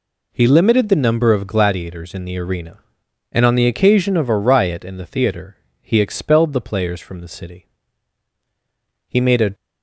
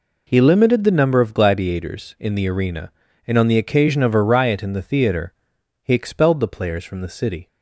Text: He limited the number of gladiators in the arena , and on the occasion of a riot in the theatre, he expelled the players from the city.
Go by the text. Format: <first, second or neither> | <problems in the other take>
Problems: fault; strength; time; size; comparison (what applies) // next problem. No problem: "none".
second | goes on to say "He made a"; slight; from 9.0 s on; 0.46 s long